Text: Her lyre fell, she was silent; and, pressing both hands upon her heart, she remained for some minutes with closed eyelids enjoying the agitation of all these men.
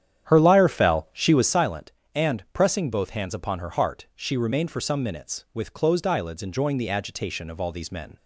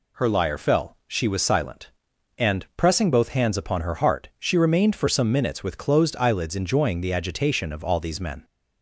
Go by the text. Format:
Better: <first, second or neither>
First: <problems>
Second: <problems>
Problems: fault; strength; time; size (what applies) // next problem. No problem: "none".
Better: second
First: starts louder than the rest; strong; until 1.6 s; 9.5 dB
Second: none